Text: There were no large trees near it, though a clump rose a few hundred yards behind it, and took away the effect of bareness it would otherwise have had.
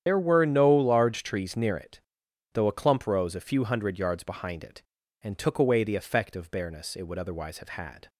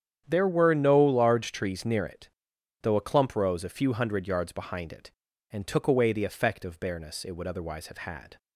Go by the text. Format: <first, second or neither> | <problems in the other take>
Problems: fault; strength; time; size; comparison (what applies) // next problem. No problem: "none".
second | loses the start of "There"; at 0.0 s; 95 ms // starts louder than the rest; strong; until 1.0 s; 9.5 dB; strong in the second